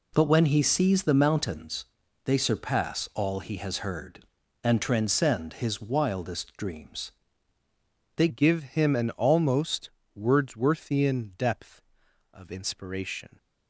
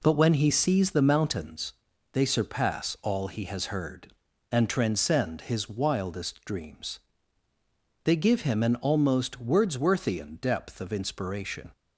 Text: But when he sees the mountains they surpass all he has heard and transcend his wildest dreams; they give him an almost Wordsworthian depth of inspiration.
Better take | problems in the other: second | pauses between "mountains" and "they"; at 1.8 s; 0.38 s long; also in the second // changes voice at "give"; from 8.2 s on; 5.1 s long // pauses between "almost" and "Wordsworthian"; slight; at 9.9 s; 0.24 s long

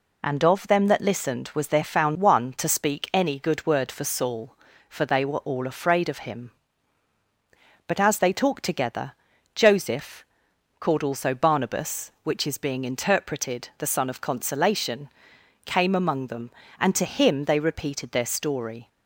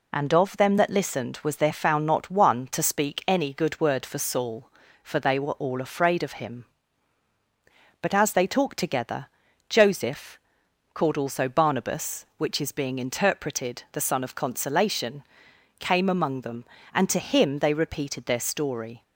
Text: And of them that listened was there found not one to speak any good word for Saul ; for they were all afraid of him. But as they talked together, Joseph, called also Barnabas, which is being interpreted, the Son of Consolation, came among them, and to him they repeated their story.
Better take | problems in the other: second | skips "not"; at 2.1 s

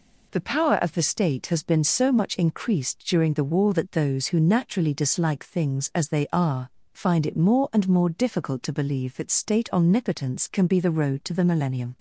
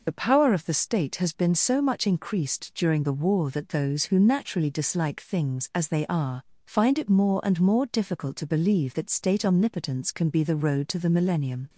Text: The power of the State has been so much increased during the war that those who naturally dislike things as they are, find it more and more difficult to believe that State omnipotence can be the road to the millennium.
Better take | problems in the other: first | loses the start of "The"; at 0.0 s; 50 ms

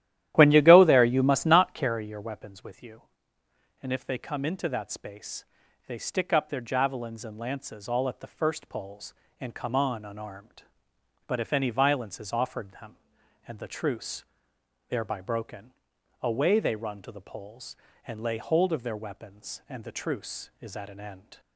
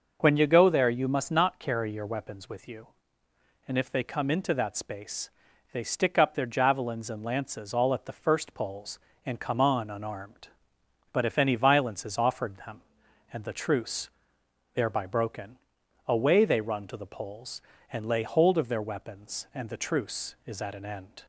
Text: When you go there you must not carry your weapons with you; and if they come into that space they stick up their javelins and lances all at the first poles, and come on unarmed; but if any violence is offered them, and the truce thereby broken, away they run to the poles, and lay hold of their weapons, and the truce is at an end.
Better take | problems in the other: second | starts louder than the rest; strong; until 2.0 s; 12.5 dB // pauses between "space" and "they"; at 5.4 s; 0.42 s long; also in the second // pauses between "truce" and "thereby"; noticeable; at 14.2 s; 0.64 s long; noticeable in the second

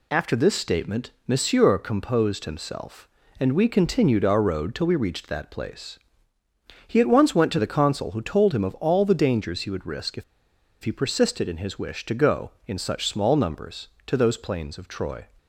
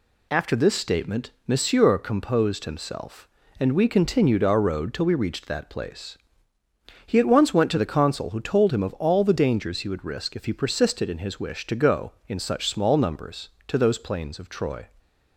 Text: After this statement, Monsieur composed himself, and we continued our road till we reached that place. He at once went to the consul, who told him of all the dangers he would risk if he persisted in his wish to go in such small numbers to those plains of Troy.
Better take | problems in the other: second | pauses between "if" and "he"; noticeable; at 10.2 s; 0.60 s long

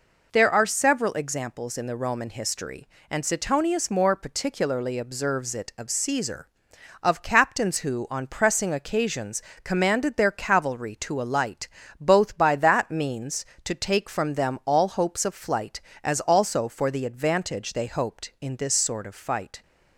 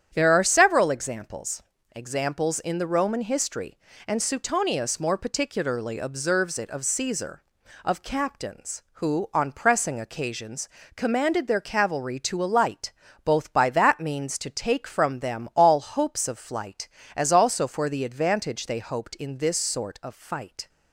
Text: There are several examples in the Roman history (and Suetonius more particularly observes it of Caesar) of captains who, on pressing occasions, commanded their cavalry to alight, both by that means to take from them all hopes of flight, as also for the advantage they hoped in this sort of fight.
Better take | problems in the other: first | starts louder than the rest; strong; until 1.1 s; 9.5 dB // says "examples" twice; at 1.9 s

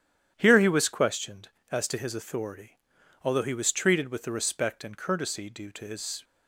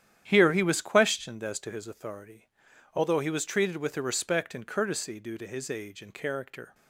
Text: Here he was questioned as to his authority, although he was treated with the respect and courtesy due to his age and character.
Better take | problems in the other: second | starts louder than the rest; strong; until 1.3 s; 10 dB; strong in the second // stops before "age and character"; at 6.2 s

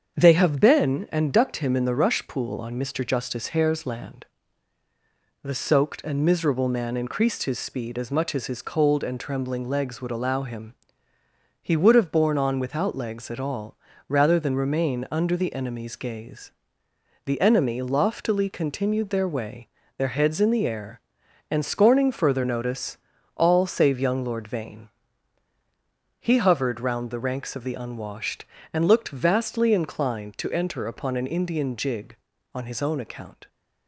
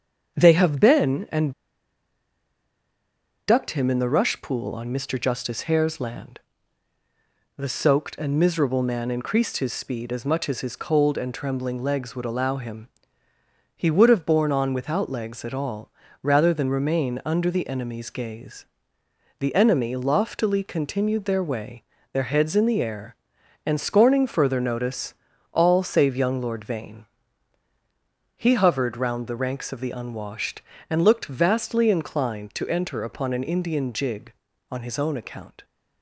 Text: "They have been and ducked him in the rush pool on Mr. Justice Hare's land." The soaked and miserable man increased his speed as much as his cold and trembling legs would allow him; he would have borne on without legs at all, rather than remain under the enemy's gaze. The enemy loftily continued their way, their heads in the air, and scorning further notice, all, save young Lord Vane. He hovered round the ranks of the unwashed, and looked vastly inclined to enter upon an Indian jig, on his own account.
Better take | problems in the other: first | starts louder than the rest; strong; until 1.3 s; 7.5 dB; strong in the first // pauses between "and" and "ducked"; strong; at 1.5 s; 1.9 s long

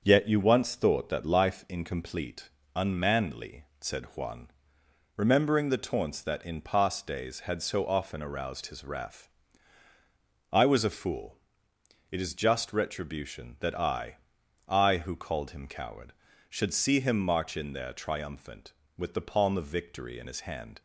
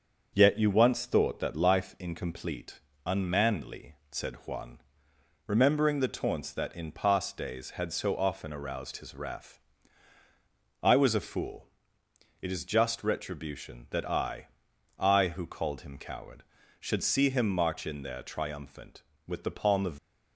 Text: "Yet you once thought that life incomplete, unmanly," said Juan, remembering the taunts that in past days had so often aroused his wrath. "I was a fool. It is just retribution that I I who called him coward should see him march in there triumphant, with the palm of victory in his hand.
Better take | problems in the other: first | starts louder than the rest; until 1.3 s; 7 dB; also in the first // pauses between "I" and "I"; noticeable; at 14.4 s; 0.50 s long; noticeable in the first // stops before "victory in his hand"; at 19.9 s

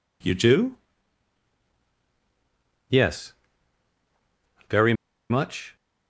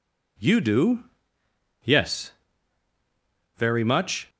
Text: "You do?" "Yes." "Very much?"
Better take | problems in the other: second | pauses between "Very" and "much"; at 4.9 s; 0.36 s long

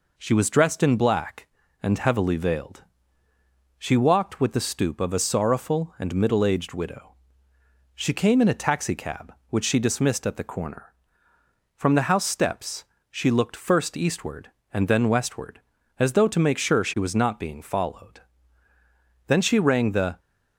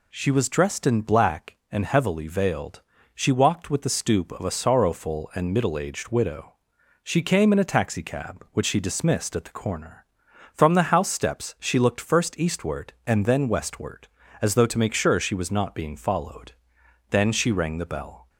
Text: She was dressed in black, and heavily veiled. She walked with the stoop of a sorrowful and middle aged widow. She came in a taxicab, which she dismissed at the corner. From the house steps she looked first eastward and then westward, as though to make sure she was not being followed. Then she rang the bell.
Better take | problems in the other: second | pauses between "steps" and "she"; slight; at 12.8 s; 0.26 s long // stops before "bell"; at 20.1 s

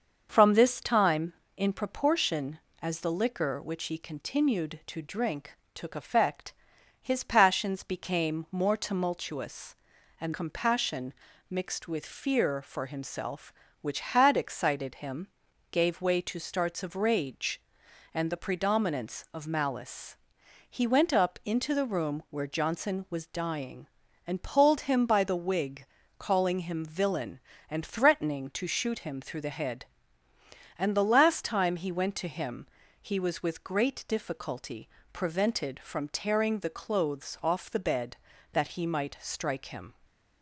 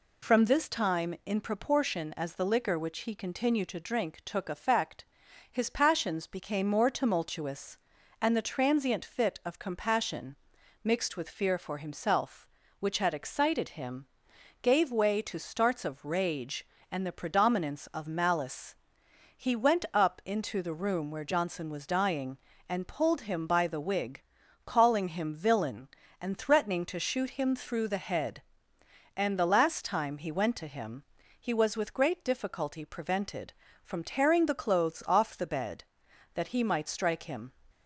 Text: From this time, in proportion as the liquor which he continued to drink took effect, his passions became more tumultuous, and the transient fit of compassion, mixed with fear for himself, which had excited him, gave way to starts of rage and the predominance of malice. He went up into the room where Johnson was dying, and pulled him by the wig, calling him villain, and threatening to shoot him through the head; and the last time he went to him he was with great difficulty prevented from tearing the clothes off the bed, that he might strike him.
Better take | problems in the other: second | starts louder than the rest; until 1.3 s; 6.5 dB // pauses between "drink" and "took"; slight; at 5.5 s; 0.18 s long // skips "the transient fit of"; at 10.3 s // pauses between "him" and "he"; slight; at 32.6 s; 0.34 s long; slight in the second // pauses between "difficulty" and "prevented"; slight; at 34.8 s; 0.26 s long // stays silent after the last word; slight; from 39.9 s on; 0.5 s long

